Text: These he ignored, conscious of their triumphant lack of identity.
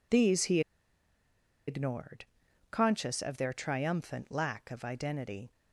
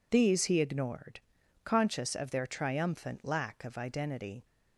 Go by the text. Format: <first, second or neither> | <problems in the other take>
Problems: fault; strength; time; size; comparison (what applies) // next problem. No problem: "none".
second | pauses between "he" and "ignored"; at 0.6 s; 1.0 s long